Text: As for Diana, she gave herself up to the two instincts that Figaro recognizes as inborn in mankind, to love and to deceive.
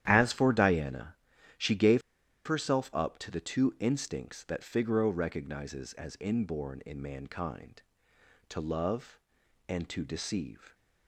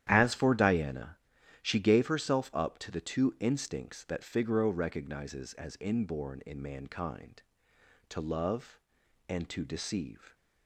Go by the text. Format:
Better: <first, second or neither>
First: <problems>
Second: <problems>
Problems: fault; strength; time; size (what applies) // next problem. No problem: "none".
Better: second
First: starts louder than the rest; strong; until 1.0 s; 11 dB // pauses between "gave" and "herself"; noticeable; at 2.0 s; 0.47 s long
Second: starts louder than the rest; strong; until 1.0 s; 11 dB